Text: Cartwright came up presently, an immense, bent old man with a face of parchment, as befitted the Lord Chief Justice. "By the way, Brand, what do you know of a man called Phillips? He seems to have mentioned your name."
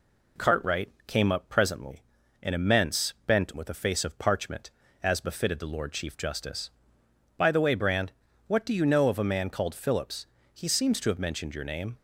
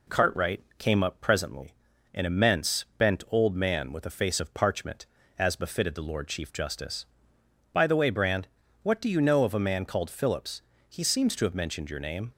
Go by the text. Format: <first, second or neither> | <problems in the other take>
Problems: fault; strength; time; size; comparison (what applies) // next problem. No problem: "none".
second | pauses between "Cartwright" and "came"; slight; at 0.8 s; 0.18 s long; slight in the second // skips "old man"; at 3.5 s